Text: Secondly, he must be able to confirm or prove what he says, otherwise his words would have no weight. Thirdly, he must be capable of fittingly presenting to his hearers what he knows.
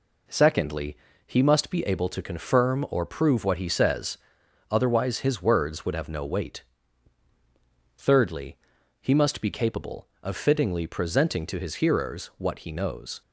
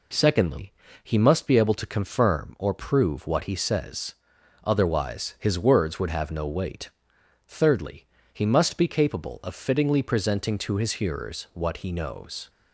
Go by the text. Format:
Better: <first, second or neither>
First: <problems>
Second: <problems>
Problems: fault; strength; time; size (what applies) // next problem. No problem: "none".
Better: neither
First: none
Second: none